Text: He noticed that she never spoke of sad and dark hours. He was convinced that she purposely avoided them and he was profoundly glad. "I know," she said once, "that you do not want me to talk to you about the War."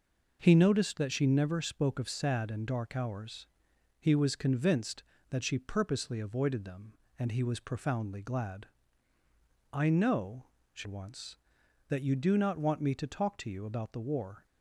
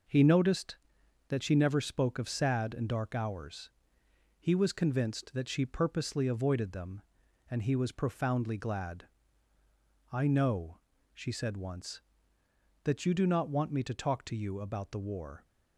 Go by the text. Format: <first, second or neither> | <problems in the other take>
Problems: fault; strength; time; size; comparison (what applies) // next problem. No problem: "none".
second | skips "said"; at 10.8 s